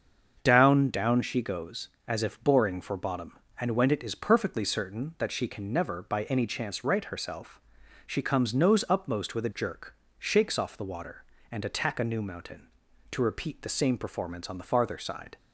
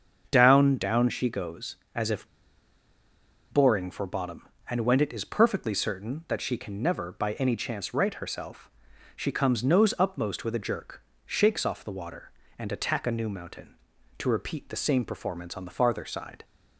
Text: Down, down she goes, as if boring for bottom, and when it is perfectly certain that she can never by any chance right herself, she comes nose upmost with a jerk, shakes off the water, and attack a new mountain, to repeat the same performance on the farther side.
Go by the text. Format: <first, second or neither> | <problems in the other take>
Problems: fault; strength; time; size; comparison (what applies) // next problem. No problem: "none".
first | starts louder than the rest; until 1.3 s; 7 dB; also in the first // pauses between "if" and "boring"; strong; at 2.2 s; 1.2 s long